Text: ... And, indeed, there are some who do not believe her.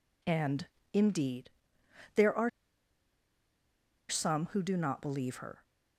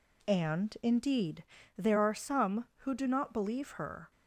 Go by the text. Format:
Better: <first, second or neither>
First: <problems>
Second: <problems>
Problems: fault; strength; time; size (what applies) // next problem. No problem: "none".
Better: second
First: pauses between "are" and "some"; strong; at 2.4 s; 1.5 s long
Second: none